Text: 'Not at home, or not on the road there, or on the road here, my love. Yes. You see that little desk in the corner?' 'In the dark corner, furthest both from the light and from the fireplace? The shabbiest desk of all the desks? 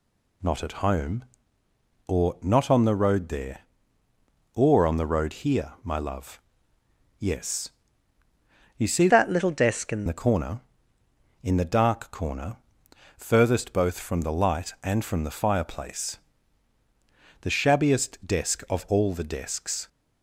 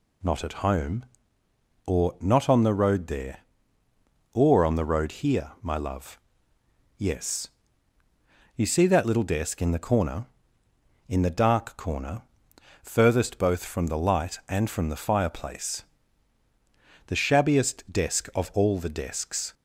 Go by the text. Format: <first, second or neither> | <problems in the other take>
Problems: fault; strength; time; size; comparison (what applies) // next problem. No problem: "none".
second | changes voice from "that" to "in"; from 9.0 to 10.0 s; 1.0 s long